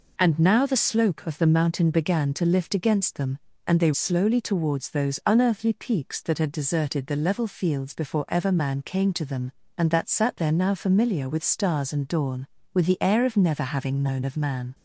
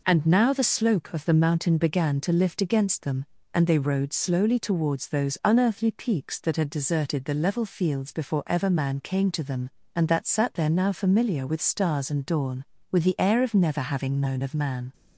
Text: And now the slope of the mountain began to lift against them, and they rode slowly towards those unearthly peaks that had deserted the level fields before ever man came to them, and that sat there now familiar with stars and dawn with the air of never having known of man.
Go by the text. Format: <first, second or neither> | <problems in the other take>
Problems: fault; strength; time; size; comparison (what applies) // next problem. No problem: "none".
second | skips "rode"; at 3.9 s